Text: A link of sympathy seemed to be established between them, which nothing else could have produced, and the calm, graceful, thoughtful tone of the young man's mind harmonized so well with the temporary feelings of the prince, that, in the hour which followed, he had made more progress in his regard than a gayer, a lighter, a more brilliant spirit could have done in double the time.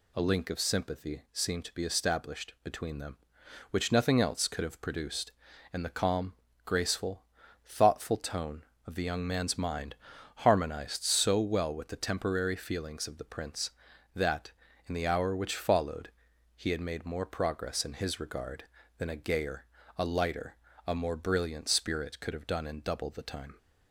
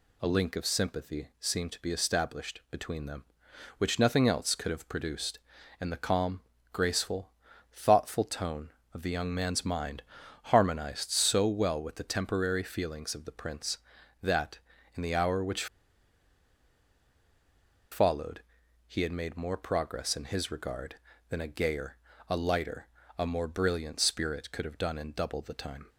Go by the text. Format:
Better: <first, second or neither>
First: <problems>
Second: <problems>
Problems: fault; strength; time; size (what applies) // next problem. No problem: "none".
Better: first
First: pauses between "mind" and "harmonized"; at 9.9 s; 0.42 s long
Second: pauses between "mind" and "harmonized"; at 10.0 s; 0.42 s long // pauses between "which" and "followed"; strong; at 15.6 s; 2.2 s long